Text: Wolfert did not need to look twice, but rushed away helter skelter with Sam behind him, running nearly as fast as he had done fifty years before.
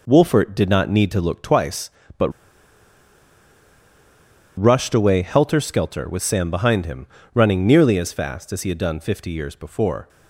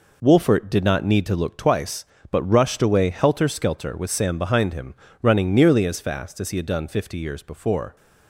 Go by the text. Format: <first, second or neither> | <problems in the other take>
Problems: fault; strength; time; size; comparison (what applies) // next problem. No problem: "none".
second | pauses between "but" and "rushed"; strong; at 2.2 s; 2.2 s long